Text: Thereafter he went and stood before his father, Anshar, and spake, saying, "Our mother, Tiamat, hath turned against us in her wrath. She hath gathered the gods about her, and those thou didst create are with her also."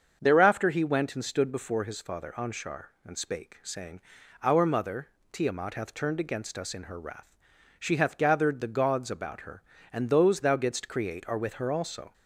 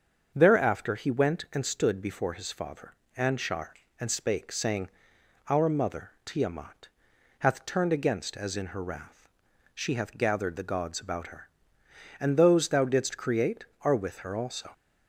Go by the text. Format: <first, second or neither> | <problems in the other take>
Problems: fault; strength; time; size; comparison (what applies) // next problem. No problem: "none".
first | starts louder than the rest; until 1.3 s; 7 dB; also in the first // says "as" for "us"; at 8.3 s